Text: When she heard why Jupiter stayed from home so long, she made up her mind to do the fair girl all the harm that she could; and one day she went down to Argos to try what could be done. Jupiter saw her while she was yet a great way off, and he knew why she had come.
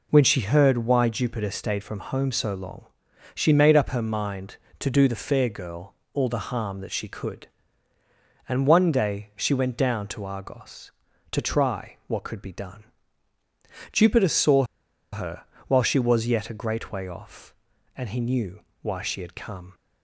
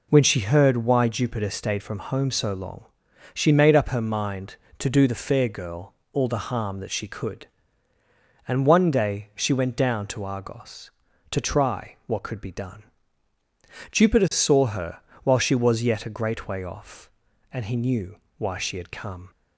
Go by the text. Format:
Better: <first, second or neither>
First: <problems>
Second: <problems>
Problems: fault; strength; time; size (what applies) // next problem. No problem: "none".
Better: second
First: pauses between "girl" and "all"; slight; at 5.9 s; 0.20 s long // pauses between "saw" and "her"; noticeable; at 14.6 s; 0.48 s long // pauses between "her" and "while"; slight; at 15.4 s; 0.24 s long // pauses between "knew" and "why"; slight; at 18.6 s; 0.20 s long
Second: pauses between "girl" and "all"; slight; at 5.9 s; 0.20 s long // pauses between "her" and "while"; slight; at 14.9 s; 0.24 s long // pauses between "knew" and "why"; slight; at 18.1 s; 0.20 s long